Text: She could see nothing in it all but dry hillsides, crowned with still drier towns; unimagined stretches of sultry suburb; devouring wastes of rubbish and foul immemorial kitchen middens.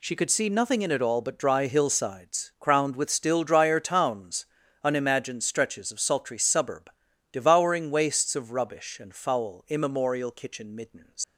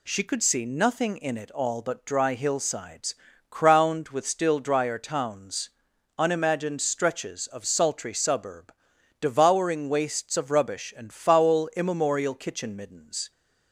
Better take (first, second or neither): second